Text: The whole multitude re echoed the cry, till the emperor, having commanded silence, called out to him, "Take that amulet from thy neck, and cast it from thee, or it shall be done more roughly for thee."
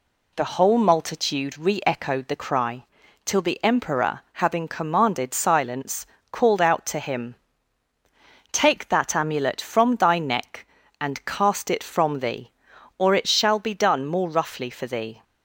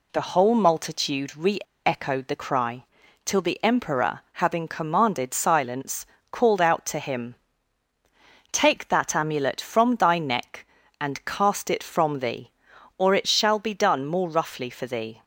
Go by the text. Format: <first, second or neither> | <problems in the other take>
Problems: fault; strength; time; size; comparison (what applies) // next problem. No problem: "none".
first | pauses between "re" and "echoed"; slight; at 1.5 s; 0.27 s long